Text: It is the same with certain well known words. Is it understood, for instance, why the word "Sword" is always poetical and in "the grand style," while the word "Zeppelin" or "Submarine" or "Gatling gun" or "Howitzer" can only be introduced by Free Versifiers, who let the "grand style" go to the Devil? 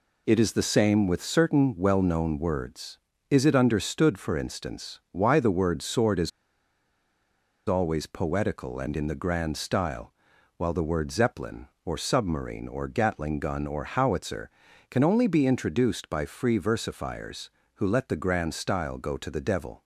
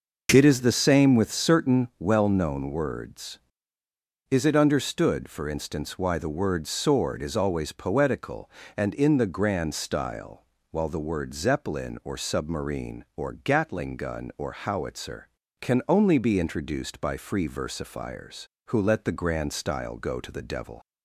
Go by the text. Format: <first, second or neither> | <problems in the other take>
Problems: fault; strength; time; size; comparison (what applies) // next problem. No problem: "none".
second | pauses between "is" and "always"; strong; at 6.3 s; 1.3 s long